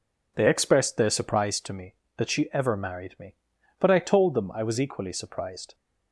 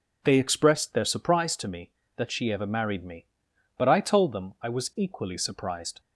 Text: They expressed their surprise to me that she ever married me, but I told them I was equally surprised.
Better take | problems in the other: neither | none

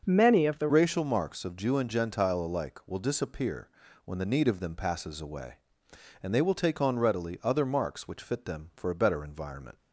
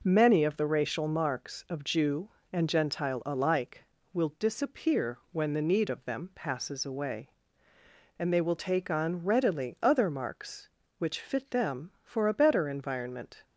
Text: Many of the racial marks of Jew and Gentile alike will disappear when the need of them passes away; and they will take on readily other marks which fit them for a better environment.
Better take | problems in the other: second | starts louder than the rest; until 1.0 s; 6 dB // changes voice at "racial"; from 0.6 s on; 9.1 s long // pauses between "disappear" and "when"; at 3.6 s; 0.38 s long

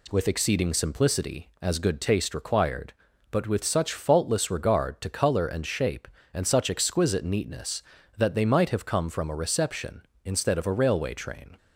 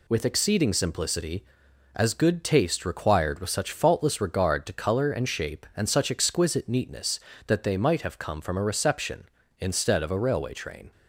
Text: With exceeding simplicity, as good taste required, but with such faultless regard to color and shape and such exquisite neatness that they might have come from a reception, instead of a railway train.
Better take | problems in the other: first | skips "but"; at 3.3 s

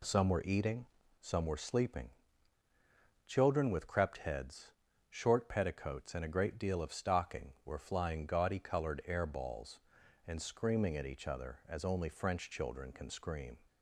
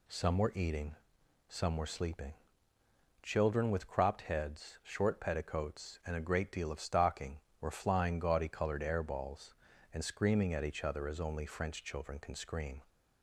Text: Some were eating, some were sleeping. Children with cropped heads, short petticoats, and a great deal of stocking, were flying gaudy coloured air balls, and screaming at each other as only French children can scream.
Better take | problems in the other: second | says "crept" for "cropped"; at 3.8 s

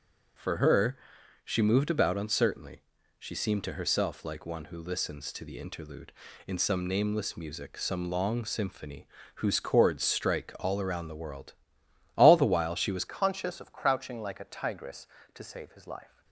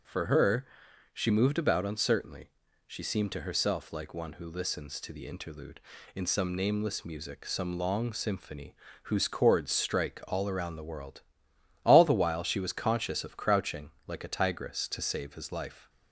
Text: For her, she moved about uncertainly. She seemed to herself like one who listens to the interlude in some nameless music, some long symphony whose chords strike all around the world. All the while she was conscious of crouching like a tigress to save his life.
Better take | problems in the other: second | starts louder than the rest; until 1.8 s; 6.5 dB // pauses between "symphony" and "whose"; slight; at 9.0 s; 0.28 s long; slight in the second // changes voice at "conscious"; from 13.0 s on; 3.2 s long

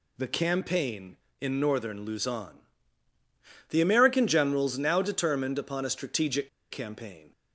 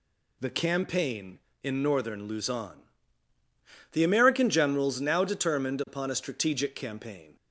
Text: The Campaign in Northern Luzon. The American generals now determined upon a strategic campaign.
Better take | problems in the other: second | pauses between "strategic" and "campaign"; slight; at 6.4 s; 0.22 s long

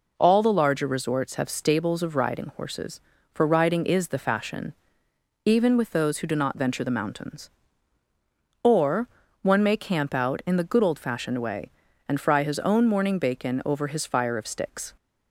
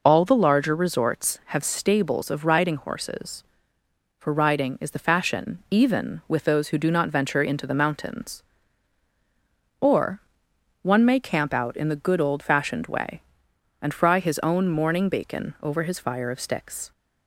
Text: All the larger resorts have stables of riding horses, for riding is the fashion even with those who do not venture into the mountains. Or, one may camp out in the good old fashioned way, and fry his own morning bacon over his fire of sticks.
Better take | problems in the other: second | pauses between "fashion" and "even"; noticeable; at 4.7 s; 0.74 s long // skips "into"; at 6.8 s

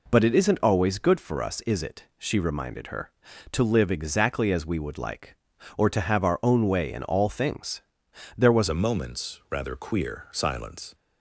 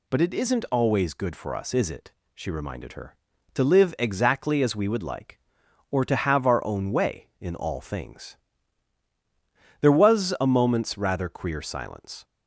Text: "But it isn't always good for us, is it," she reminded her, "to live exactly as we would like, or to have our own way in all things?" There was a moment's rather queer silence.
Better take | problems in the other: second | changes voice at "a"; from 8.6 s on; 2.3 s long

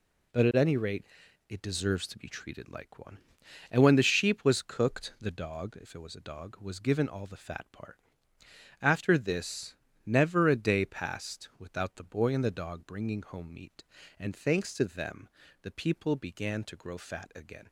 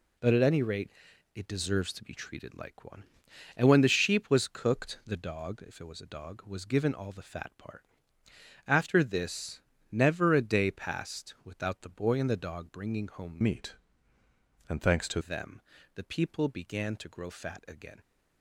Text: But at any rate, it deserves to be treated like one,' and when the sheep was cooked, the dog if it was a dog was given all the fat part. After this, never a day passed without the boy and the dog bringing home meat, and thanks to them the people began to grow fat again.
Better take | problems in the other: first | changes voice from "meat" to "to"; from 13.4 to 15.2 s; 1.8 s long // pauses between "them" and "the"; slight; at 15.5 s; 0.36 s long; slight in the first

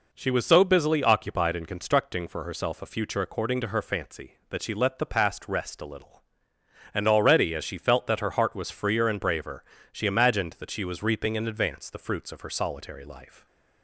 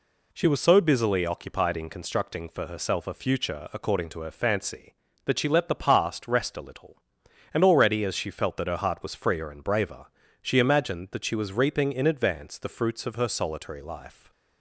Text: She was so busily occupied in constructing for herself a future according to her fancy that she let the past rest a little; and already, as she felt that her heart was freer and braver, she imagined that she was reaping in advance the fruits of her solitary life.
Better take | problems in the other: neither | none

